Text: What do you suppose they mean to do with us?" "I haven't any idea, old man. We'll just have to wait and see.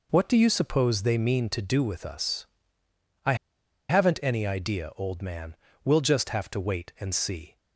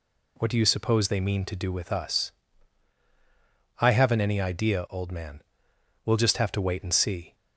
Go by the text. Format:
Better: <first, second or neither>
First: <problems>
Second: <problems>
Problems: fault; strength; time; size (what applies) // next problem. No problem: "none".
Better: second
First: pauses between "I" and "haven't"; noticeable; at 3.3 s; 0.54 s long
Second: none